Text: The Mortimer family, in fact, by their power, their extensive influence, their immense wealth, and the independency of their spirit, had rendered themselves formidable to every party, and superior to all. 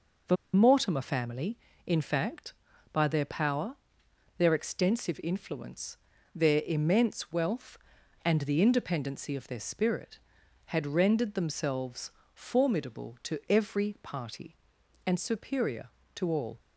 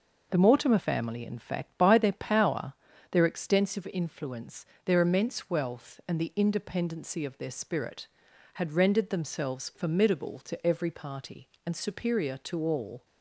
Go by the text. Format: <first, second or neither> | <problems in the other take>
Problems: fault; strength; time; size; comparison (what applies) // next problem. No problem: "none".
second | pauses between "The" and "Mortimer"; slight; at 0.3 s; 0.17 s long // pauses between "themselves" and "formidable"; slight; at 12.0 s; 0.24 s long